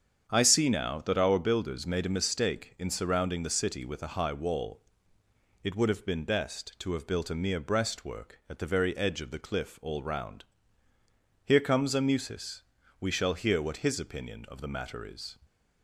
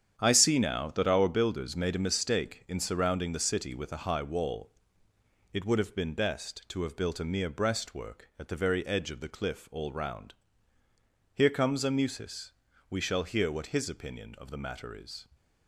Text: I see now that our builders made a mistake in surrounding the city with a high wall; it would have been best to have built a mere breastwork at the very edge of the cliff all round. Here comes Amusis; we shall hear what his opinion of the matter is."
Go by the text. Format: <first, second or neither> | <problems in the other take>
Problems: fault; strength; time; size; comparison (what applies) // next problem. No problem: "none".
first | gets quieter; strong; throughout; 9 dB // starts louder than the rest; strong; until 1.2 s; 9 dB; strong in the first